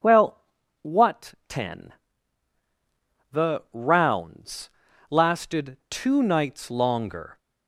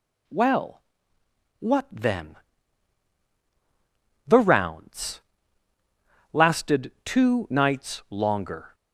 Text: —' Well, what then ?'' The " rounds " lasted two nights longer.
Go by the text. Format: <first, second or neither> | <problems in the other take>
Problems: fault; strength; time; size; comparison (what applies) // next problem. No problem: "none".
second | starts louder than the rest; until 1.5 s; 7 dB // says "ten" for "then"; at 1.4 s